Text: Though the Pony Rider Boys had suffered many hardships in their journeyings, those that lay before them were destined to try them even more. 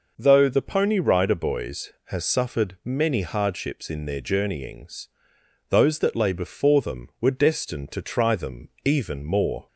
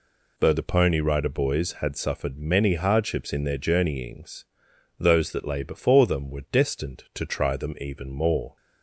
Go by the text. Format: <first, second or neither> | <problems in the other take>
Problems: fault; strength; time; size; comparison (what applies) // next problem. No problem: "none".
second | says "has" for "had"; at 2.0 s // pauses between "them" and "even"; slight; at 8.6 s; 0.16 s long